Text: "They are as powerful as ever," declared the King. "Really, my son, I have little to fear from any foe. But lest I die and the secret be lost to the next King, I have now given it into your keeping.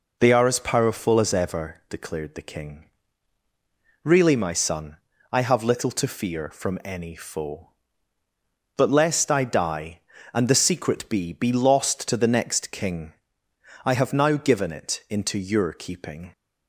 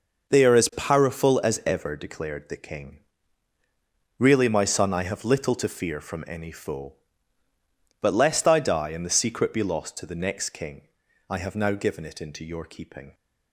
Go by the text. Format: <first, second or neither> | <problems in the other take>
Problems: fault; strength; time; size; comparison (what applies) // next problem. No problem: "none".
second | says "be" twice; at 11.3 s